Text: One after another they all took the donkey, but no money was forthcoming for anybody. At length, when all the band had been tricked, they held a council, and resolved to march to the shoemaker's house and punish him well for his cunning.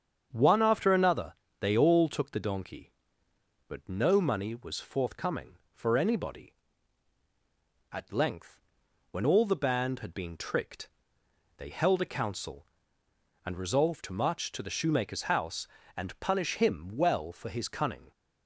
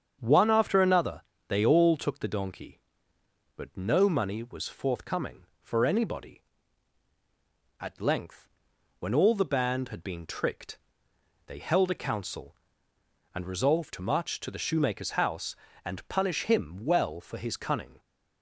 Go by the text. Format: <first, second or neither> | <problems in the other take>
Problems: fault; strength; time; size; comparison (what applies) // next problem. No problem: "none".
neither | starts louder than the rest; strong; the same in both // pauses between "another" and "they"; slight; the same in both